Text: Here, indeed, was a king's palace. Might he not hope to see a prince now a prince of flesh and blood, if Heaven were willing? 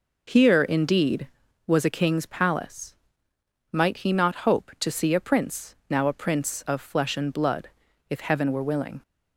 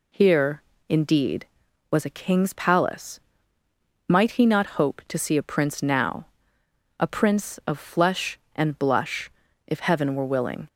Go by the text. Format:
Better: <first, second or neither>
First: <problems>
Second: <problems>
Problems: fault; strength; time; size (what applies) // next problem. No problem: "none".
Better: first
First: none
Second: pauses between "now" and "a"; noticeable; at 6.2 s; 0.74 s long // says "blush" for "blood"; at 8.7 s